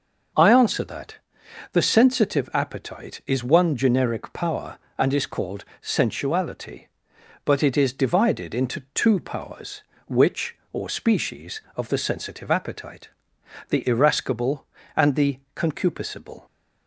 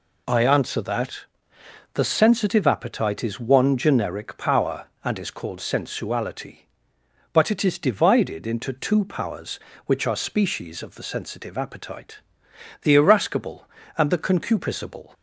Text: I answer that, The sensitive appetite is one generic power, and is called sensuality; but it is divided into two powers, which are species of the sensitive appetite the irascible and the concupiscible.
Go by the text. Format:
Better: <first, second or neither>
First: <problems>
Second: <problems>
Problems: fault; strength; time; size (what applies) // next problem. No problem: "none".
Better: second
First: pauses between "called" and "sensuality"; slight; at 5.6 s; 0.18 s long // says "or" for "are"; at 10.7 s // pauses between "appetite" and "the"; noticeable; at 13.0 s; 0.60 s long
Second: pauses between "appetite" and "the"; noticeable; at 12.1 s; 0.64 s long